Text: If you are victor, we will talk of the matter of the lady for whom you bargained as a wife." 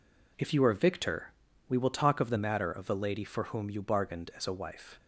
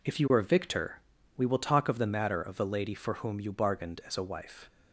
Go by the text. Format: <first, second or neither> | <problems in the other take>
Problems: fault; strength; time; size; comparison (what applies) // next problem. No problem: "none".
neither | none